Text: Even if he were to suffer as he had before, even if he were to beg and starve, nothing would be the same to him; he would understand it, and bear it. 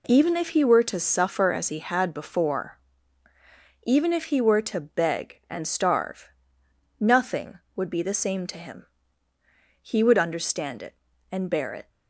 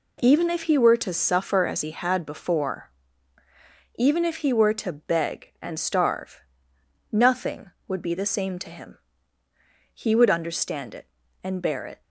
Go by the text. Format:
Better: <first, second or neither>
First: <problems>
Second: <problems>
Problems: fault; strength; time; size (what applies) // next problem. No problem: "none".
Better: neither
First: none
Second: none